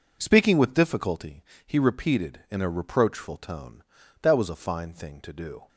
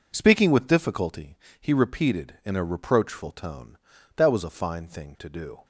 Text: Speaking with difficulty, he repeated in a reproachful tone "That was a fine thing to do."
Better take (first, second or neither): neither